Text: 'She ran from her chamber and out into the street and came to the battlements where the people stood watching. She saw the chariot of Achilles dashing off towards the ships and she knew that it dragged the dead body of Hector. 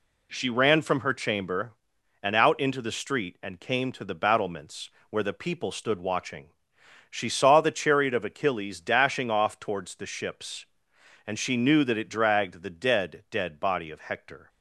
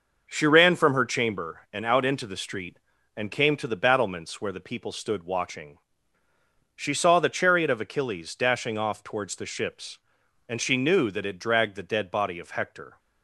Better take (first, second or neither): second